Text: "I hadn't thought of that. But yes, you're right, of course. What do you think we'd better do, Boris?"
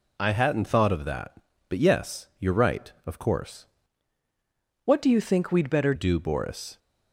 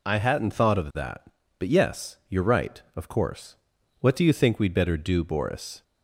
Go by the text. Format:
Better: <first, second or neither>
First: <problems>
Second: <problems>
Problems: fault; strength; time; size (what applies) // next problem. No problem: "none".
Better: second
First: changes voice from "What" to "better"; from 4.8 to 5.9 s; 1.1 s long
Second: none